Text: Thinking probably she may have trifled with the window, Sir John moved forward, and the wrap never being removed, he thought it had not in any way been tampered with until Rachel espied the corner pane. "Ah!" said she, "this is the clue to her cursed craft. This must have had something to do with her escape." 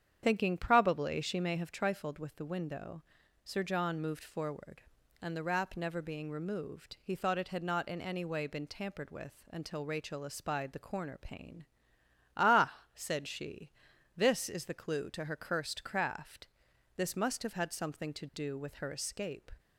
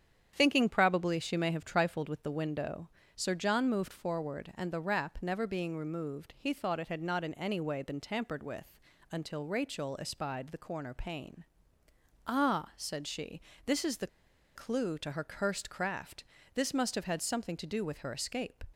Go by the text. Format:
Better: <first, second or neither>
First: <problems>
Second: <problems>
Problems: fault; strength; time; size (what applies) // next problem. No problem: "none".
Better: first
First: starts louder than the rest; strong; until 1.2 s; 8.5 dB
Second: starts louder than the rest; strong; until 1.3 s; 8.5 dB // pauses between "with" and "until"; slight; at 8.7 s; 0.36 s long // pauses between "the" and "clue"; noticeable; at 14.0 s; 0.47 s long